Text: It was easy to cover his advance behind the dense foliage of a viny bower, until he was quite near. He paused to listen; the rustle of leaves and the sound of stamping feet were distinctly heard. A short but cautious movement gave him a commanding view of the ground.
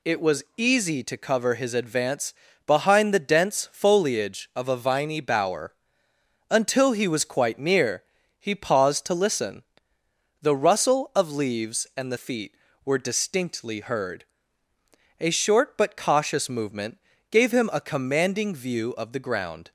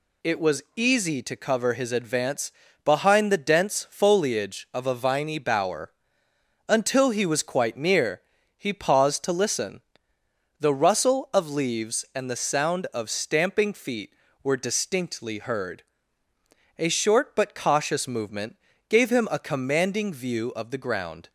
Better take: second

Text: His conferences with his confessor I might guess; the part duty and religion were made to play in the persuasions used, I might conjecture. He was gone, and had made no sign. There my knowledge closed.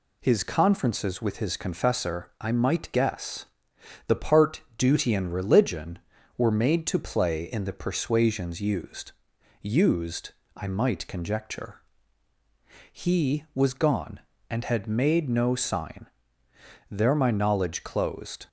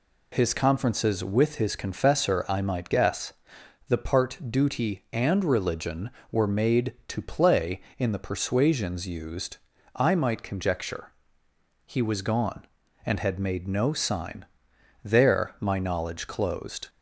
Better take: second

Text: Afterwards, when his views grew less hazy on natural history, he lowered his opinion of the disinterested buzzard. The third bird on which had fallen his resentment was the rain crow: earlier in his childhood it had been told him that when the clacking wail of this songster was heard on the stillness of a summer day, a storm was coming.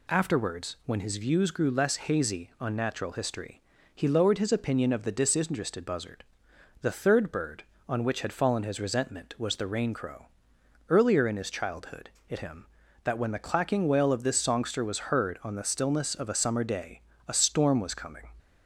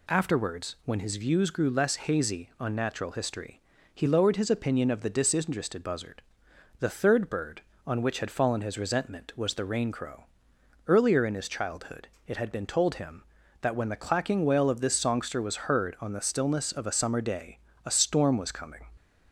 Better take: second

